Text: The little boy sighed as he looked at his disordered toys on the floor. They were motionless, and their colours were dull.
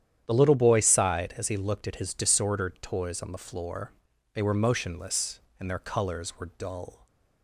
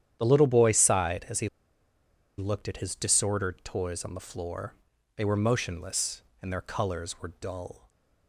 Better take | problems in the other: first | starts louder than the rest; strong; until 1.2 s; 10 dB; strong in the first // pauses between "he" and "looked"; noticeable; at 1.4 s; 0.89 s long

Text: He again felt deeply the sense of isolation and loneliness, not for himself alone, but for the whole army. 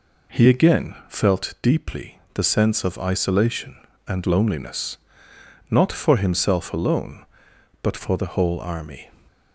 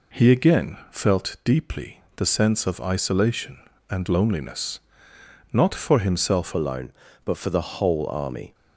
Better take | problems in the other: first | changes voice at "alone"; from 6.5 s on; 2.0 s long

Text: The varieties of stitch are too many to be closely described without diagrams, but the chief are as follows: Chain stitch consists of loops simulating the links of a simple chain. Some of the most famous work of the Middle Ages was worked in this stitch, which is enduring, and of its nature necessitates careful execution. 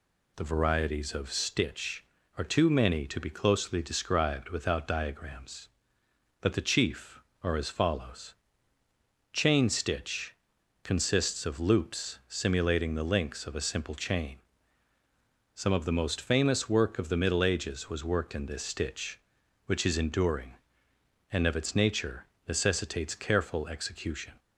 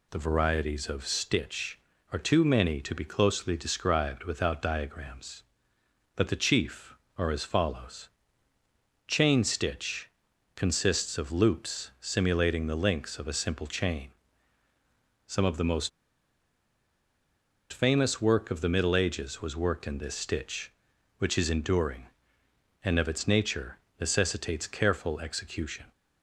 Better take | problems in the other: first | pauses between "stitch" and "consists"; noticeable; at 10.0 s; 0.46 s long; noticeable in the first // pauses between "most" and "famous"; strong; at 15.8 s; 1.8 s long // pauses between "nature" and "necessitates"; slight; at 23.7 s; 0.20 s long; slight in the first

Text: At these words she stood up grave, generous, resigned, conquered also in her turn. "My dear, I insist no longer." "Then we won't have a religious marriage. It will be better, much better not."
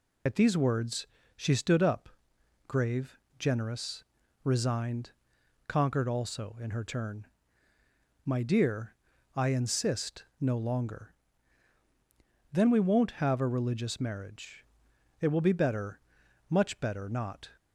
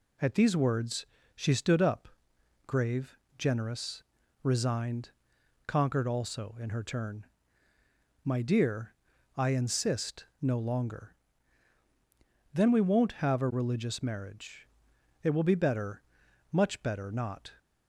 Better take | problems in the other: second | loses the start of "At"; at 0.2 s; 50 ms // pauses between "words" and "she"; slight; at 1.0 s; 0.30 s long; slight in the second // pauses between "up" and "grave"; noticeable; at 2.0 s; 0.58 s long; noticeable in the second

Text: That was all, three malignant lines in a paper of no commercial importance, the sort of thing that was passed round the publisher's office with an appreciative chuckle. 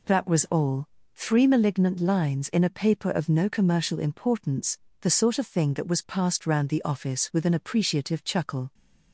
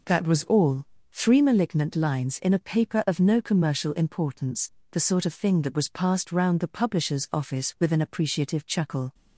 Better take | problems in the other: second | skips "publisher's"; at 6.8 s

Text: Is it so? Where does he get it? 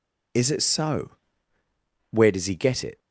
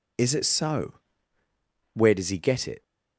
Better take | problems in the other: neither | none

